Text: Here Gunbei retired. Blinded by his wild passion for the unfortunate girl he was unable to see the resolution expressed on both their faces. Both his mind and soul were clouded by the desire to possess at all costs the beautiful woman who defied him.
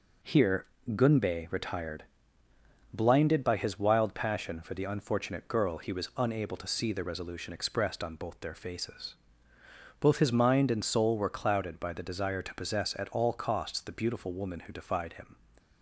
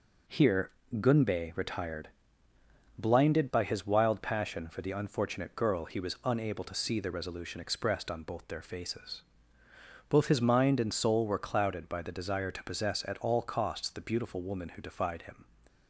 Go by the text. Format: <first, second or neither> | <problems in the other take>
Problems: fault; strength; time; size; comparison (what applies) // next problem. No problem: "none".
neither | pauses between "Here" and "Gunbei"; slight; the same in both